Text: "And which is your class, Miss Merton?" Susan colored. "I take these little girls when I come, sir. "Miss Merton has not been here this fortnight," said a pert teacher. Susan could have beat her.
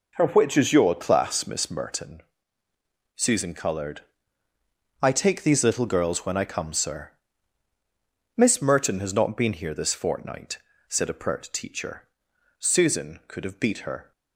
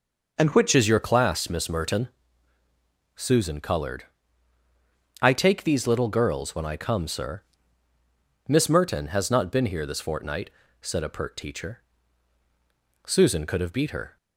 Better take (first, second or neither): first